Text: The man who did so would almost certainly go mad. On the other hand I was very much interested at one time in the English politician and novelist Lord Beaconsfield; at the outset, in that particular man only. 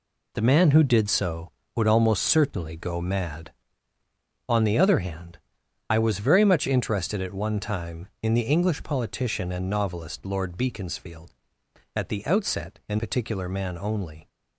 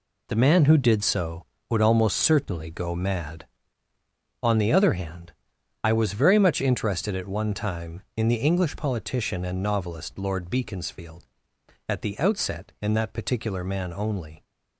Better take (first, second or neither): second